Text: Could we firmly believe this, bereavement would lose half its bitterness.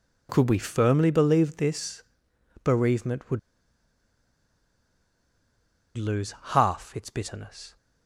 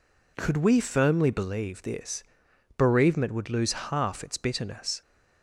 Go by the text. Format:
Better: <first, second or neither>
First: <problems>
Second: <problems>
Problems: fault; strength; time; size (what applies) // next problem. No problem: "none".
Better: second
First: pauses between "would" and "lose"; strong; at 3.3 s; 2.5 s long // pauses between "lose" and "half"; slight; at 6.3 s; 0.18 s long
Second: none